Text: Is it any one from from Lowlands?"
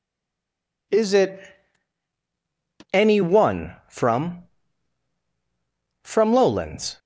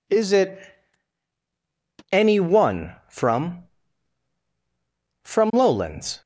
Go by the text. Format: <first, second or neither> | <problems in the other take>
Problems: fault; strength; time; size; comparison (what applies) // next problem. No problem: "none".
second | stays silent before the first word; slight; until 0.8 s; 0.8 s long // pauses between "it" and "any"; strong; at 1.3 s; 1.5 s long; strong in the second